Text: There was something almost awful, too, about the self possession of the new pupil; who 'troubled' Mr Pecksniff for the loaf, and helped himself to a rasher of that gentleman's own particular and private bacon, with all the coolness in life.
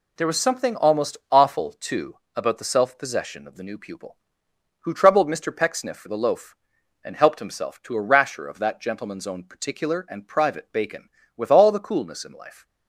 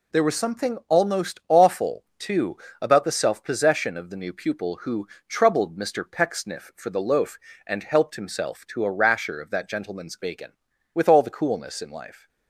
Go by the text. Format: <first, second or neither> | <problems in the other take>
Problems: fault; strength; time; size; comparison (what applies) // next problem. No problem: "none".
first | pauses between "who" and "troubled"; slight; at 5.0 s; 0.22 s long // skips "own particular and private"; at 10.1 s